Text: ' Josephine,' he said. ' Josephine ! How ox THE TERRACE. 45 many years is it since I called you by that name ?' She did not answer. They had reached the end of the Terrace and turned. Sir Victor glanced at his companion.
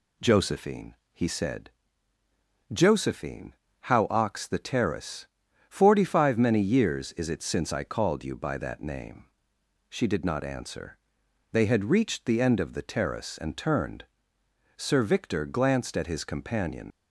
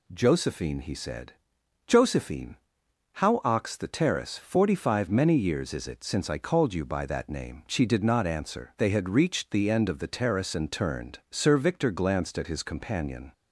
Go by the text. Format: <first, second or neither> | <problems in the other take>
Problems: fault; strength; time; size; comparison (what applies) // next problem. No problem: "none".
second | leaves "companion" unfinished; at 16.9 s; 105 ms